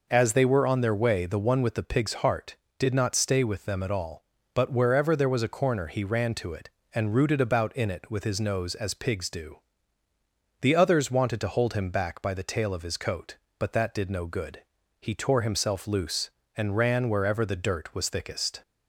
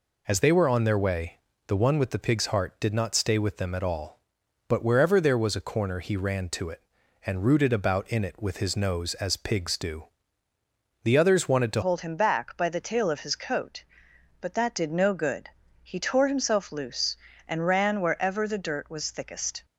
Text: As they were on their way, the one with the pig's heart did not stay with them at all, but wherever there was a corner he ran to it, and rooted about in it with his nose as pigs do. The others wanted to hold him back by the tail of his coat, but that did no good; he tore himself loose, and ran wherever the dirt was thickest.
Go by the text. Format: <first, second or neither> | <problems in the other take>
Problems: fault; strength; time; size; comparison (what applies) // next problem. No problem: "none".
first | changes voice at "hold"; from 11.8 s on; 7.8 s long